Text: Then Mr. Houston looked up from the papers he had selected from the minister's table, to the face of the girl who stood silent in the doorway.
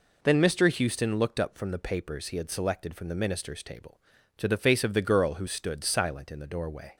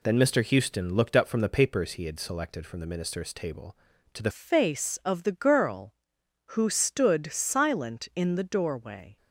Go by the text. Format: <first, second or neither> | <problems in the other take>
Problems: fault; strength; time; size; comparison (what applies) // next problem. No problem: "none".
first | changes voice at "face"; from 4.3 s on; 4.8 s long